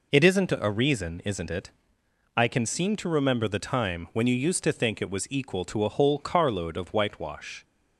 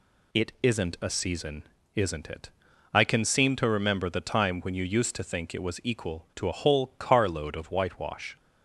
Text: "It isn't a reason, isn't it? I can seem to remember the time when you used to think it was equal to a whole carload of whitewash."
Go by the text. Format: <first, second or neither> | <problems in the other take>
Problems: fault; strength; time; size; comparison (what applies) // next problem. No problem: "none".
first | says "season" for "reason"; at 1.0 s